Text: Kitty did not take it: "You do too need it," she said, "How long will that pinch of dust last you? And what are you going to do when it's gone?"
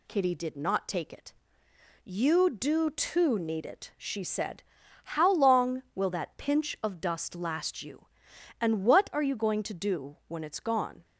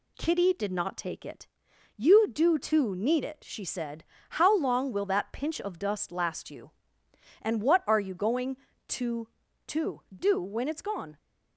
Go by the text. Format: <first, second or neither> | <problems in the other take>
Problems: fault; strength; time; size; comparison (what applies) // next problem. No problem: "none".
first | says "to" twice; at 9.6 s